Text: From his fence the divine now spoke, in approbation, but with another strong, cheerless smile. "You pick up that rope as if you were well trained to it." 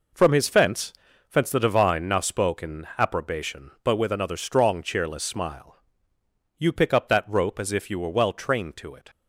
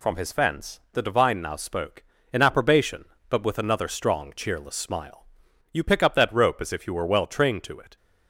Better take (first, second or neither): second